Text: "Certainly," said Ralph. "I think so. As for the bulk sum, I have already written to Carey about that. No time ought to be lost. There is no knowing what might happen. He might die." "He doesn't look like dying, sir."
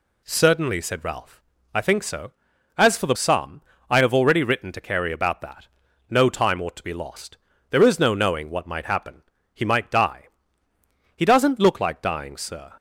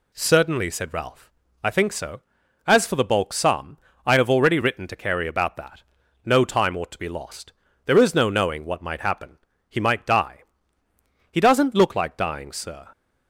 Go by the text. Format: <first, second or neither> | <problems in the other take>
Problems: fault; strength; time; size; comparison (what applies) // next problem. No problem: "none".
second | skips "bulk"; at 3.1 s